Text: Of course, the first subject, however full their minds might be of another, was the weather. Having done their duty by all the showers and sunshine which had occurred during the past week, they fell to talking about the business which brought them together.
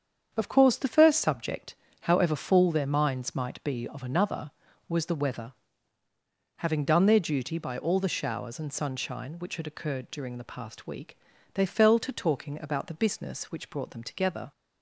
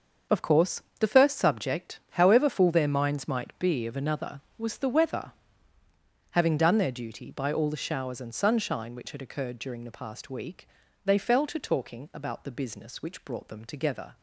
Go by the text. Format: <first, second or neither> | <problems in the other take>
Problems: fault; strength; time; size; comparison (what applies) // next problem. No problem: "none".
neither | starts louder than the rest; the same in both